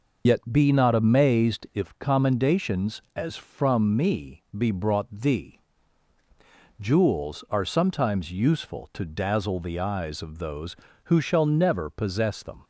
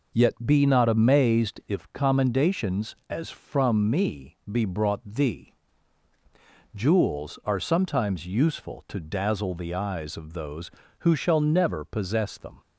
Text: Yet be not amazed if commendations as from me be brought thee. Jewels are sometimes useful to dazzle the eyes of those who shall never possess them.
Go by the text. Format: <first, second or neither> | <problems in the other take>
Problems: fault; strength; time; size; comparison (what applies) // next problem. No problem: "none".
second | loses the start of "Yet"; at 0.2 s; 55 ms